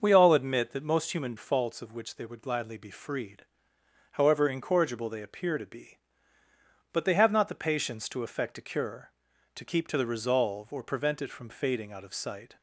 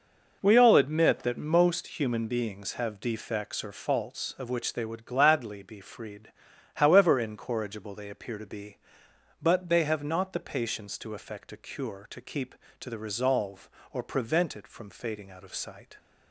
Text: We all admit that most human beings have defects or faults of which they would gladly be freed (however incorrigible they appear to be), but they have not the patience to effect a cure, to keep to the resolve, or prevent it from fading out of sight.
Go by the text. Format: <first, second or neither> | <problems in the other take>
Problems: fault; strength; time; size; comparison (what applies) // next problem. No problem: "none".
second | starts louder than the rest; noticeable; until 1.0 s; 6 dB // skips "beings have defects or"; at 1.3 s